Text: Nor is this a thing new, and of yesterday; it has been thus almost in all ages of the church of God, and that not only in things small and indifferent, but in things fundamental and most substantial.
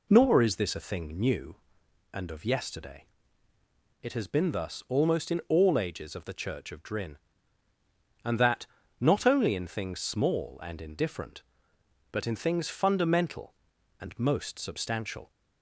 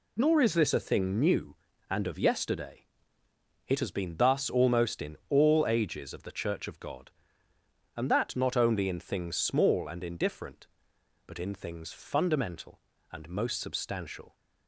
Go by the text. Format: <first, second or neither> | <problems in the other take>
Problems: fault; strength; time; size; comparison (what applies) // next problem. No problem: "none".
second | says "Drin" for "God"; at 6.8 s // pauses between "that" and "not"; slight; at 8.6 s; 0.36 s long